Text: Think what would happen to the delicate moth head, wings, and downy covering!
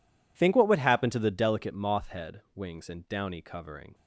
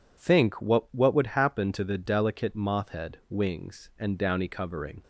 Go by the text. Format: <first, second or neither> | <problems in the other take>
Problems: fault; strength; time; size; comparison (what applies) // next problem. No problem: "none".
first | says "what" twice; at 0.9 s